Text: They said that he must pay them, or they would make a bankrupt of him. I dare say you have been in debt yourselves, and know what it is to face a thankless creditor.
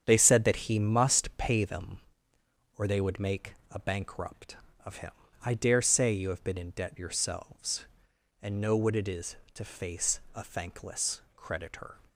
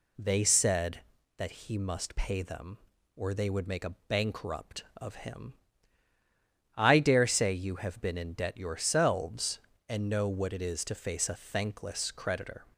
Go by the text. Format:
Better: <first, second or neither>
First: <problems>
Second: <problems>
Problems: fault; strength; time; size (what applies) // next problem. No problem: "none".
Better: second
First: gets quieter; strong; throughout; 8 dB // pauses between "make" and "a"; slight; at 3.5 s; 0.18 s long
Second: none